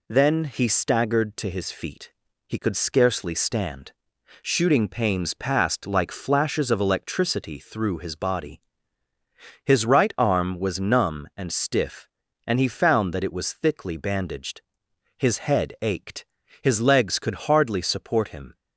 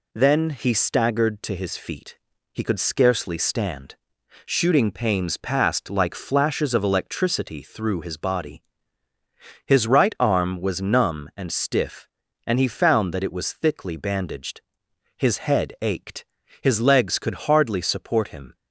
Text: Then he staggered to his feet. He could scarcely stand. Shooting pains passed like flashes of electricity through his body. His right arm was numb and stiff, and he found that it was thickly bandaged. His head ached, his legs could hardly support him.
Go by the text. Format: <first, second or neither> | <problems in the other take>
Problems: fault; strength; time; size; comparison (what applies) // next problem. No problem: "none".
neither | none